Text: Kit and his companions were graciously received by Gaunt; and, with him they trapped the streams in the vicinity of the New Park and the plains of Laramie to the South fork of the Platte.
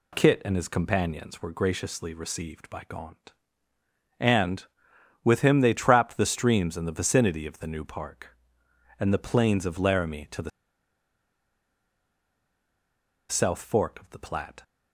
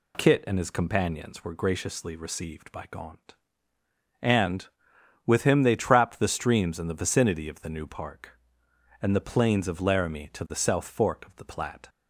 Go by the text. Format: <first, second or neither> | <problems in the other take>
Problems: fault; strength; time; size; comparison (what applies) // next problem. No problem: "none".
second | pauses between "the" and "South"; strong; at 10.5 s; 2.8 s long